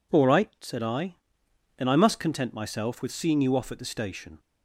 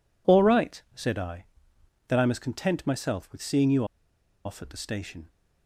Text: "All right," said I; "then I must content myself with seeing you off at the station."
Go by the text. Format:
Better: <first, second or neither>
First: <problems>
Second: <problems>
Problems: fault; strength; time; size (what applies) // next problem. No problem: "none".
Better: first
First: none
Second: pauses between "you" and "off"; noticeable; at 3.8 s; 0.60 s long